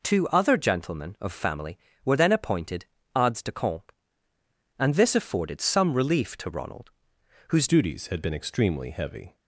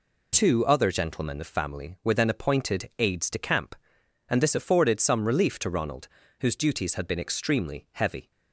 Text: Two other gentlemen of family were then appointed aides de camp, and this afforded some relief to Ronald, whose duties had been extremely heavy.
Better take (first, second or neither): second